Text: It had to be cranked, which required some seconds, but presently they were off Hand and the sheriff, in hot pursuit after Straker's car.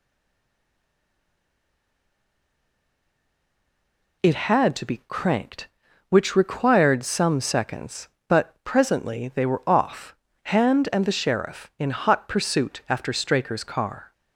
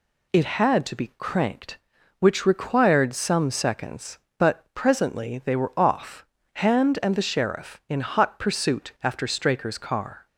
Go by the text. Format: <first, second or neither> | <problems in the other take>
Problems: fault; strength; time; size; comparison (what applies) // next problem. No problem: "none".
second | stays silent before the first word; strong; until 4.2 s; 4.2 s long // pauses between "off" and "Hand"; slight; at 10.1 s; 0.32 s long; slight in the second